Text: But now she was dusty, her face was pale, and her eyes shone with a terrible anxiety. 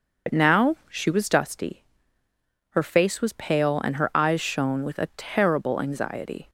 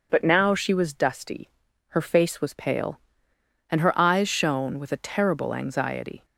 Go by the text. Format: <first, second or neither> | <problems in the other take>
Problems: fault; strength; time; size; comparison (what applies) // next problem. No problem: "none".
second | loses the start of "But"; at 0.2 s; 70 ms // starts louder than the rest; noticeable; until 1.4 s; 6 dB